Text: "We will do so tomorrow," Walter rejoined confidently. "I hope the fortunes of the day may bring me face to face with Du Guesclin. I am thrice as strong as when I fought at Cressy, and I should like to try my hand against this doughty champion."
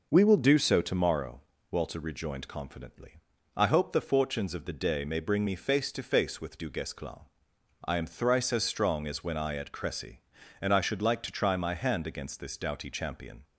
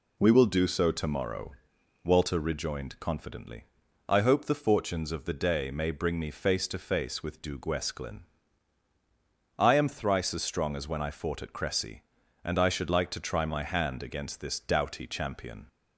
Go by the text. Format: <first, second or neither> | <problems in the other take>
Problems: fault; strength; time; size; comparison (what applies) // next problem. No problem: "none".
second | skips "fought"; at 9.5 s